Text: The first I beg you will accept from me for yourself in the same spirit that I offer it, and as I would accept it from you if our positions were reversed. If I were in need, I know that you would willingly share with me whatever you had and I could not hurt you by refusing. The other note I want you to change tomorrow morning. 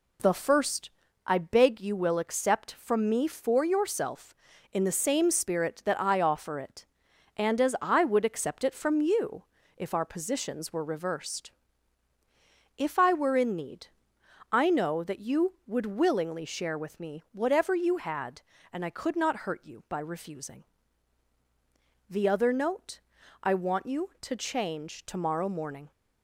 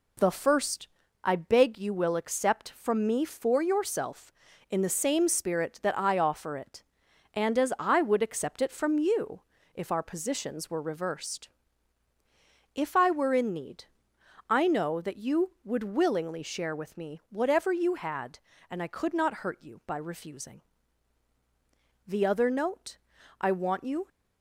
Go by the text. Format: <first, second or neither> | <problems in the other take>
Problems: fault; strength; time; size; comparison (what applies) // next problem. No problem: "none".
first | pauses between "first" and "I"; slight; at 0.8 s; 0.34 s long; slight in the first // pauses between "you" and "if"; slight; at 9.4 s; 0.32 s long; slight in the first // pauses between "note" and "I"; at 22.9 s; 0.44 s long; also in the first // stops before "to change tomorrow morning"; at 24.0 s